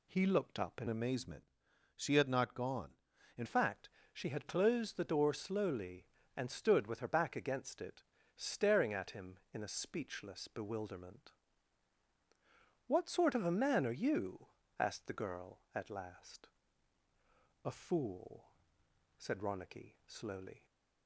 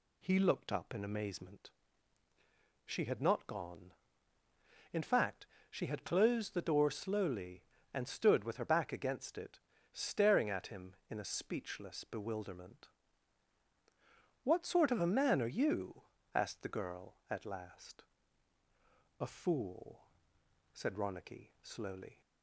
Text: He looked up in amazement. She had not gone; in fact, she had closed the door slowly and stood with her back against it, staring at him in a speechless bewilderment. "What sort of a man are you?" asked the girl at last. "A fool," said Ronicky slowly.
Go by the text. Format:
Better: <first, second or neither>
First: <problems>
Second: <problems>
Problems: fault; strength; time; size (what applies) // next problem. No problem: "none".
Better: second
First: changes voice from "amazement" to "in"; from 0.8 to 3.4 s; 2.6 s long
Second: none